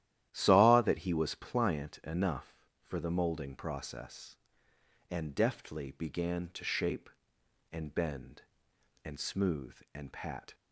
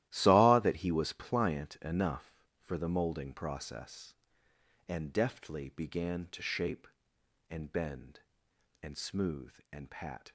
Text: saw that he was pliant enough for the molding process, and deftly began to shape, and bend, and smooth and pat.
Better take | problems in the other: first | gets quieter; strong; throughout; 13 dB // starts louder than the rest; strong; until 1.1 s; 14 dB; strong in the first

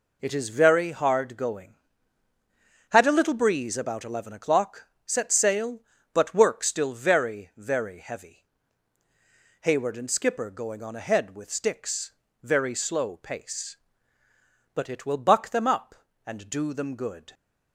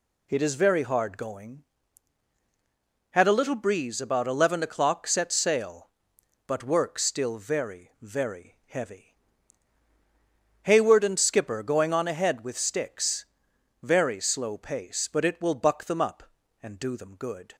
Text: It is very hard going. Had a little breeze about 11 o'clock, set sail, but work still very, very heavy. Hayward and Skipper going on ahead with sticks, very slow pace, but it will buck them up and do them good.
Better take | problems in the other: neither | none

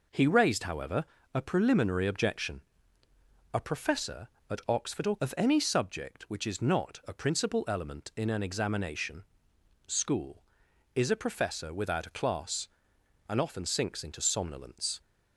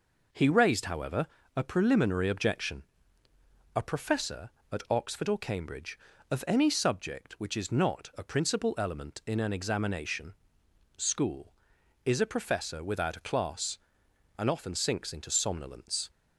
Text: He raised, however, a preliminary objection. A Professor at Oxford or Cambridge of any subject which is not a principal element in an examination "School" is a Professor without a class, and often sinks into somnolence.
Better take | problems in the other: second | skips "Cambridge"; at 5.1 s // pauses between "examination" and "School"; noticeable; at 9.2 s; 0.64 s long; noticeable in the second

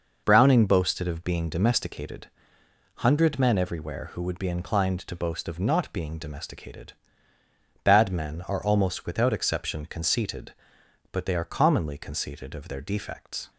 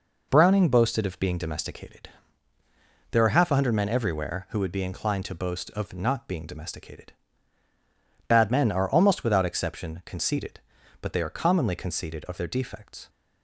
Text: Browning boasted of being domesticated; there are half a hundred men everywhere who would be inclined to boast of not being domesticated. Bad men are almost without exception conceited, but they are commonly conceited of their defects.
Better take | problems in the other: second | skips "there are half a"; at 2.6 s

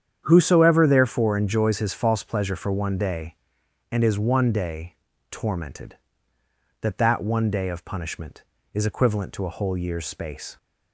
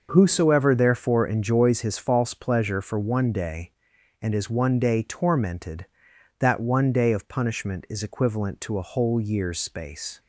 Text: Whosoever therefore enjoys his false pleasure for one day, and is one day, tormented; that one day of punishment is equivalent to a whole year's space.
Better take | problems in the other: second | starts louder than the rest; strong; until 1.2 s; 8.5 dB // says "that" twice; at 6.9 s

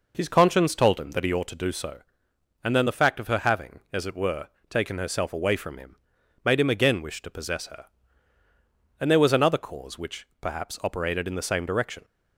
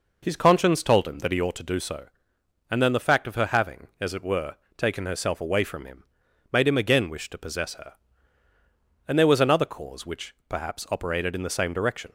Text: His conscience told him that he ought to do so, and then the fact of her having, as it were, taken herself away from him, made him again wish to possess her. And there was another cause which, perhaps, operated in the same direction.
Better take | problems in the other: neither | none

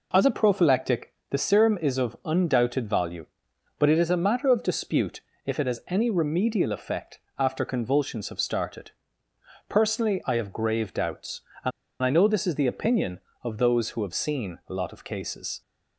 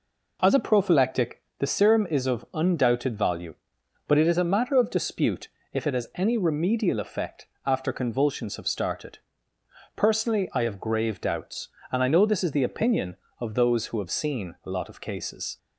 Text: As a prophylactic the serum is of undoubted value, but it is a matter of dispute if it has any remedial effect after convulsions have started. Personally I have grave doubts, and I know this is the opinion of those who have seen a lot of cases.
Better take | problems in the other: second | pauses between "prophylactic" and "the"; slight; at 1.1 s; 0.16 s long; slight in the second // pauses between "dispute" and "if"; slight; at 5.2 s; 0.24 s long; slight in the second // pauses between "effect" and "after"; slight; at 7.1 s; 0.20 s long; slight in the second // pauses between "and" and "I"; slight; at 11.7 s; 0.32 s long

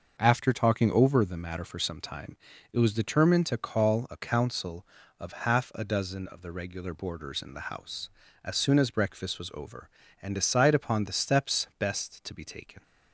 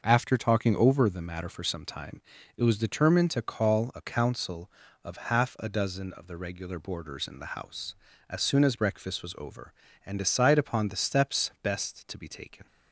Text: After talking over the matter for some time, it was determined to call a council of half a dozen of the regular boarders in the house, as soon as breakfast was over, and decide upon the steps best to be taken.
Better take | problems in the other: neither | starts louder than the rest; noticeable; the same in both

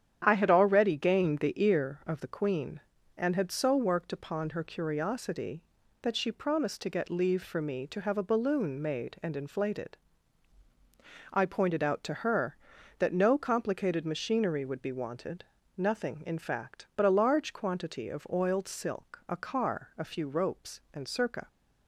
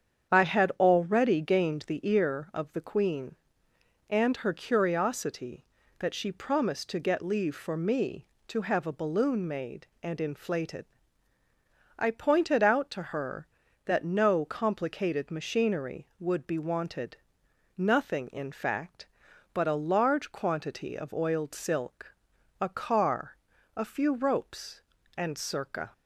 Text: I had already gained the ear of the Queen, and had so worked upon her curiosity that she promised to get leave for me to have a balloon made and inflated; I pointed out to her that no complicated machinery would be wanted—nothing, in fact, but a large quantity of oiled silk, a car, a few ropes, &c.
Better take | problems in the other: first | starts louder than the rest; strong; until 1.3 s; 8 dB; strong in the first // skips "had so worked upon"; at 4.3 s

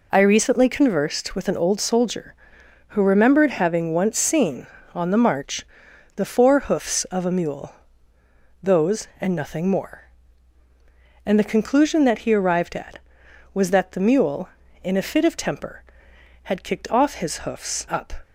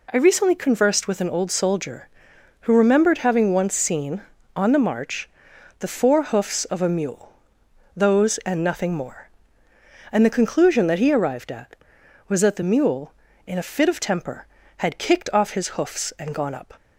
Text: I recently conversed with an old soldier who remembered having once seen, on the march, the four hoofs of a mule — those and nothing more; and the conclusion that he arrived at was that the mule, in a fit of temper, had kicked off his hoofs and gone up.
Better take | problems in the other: second | skips "and gone"; at 17.8 s

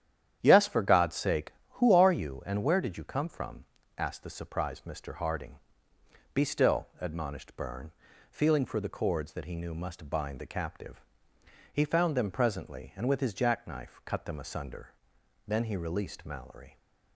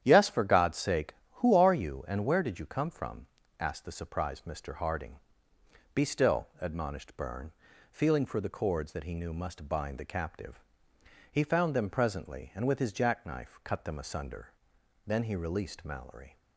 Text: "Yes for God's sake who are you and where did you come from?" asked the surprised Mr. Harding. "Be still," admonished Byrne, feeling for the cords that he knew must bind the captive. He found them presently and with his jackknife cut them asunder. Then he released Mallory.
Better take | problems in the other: neither | starts louder than the rest; strong; the same in both

